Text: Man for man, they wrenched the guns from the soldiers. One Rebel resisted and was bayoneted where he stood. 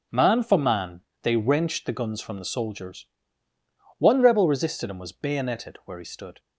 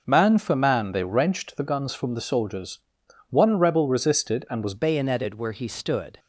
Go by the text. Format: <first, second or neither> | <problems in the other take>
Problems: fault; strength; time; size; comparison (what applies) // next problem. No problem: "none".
first | changes voice at "bayoneted"; from 4.7 s on; 1.4 s long